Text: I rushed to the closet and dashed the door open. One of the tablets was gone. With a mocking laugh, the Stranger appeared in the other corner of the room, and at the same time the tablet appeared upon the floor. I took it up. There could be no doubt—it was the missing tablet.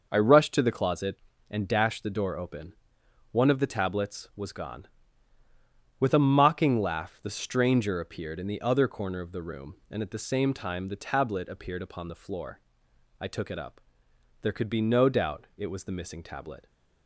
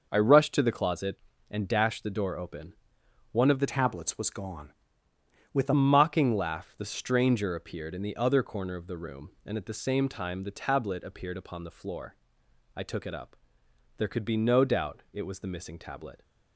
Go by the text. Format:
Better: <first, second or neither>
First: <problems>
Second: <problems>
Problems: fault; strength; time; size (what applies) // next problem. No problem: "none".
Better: first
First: none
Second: changes voice from "tablets" to "a"; from 3.6 to 5.7 s; 2.1 s long